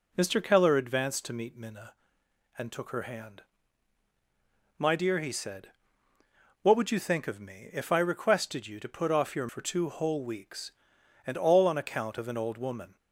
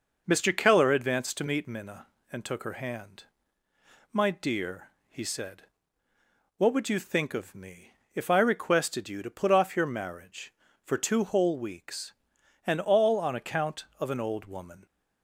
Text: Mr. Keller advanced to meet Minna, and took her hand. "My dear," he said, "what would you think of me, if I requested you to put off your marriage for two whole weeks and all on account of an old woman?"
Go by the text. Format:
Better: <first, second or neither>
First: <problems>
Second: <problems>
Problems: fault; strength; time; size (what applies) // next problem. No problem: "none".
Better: second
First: skips "marriage"; at 9.4 s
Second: none